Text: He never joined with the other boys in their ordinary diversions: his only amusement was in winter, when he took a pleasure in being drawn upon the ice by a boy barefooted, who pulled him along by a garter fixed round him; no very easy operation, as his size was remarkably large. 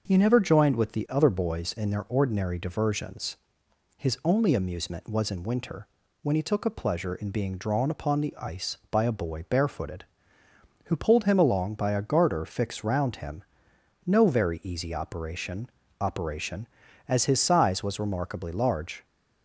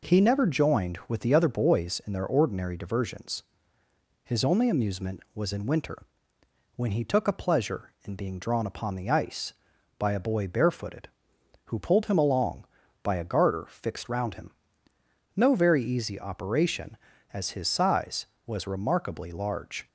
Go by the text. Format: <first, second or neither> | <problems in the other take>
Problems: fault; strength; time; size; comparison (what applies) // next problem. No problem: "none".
second | starts louder than the rest; until 1.0 s; 6 dB // says "operation" twice; at 16.0 s